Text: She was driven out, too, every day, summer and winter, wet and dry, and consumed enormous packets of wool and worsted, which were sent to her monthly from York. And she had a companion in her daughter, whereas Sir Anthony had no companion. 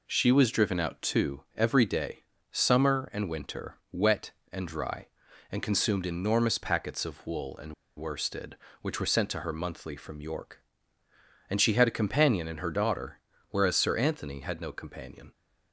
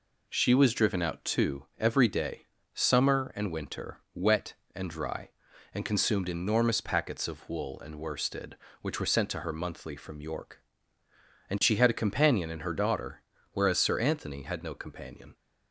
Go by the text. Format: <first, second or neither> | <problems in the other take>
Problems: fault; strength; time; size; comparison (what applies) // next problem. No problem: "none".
second | pauses between "and" and "worsted"; slight; at 7.7 s; 0.24 s long